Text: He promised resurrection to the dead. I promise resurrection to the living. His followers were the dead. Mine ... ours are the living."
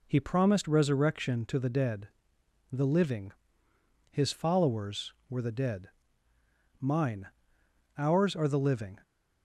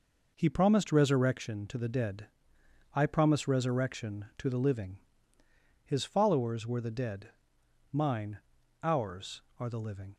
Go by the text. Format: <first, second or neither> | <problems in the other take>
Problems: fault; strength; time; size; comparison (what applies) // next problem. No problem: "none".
second | skips "I promise resurrection to"; at 2.4 s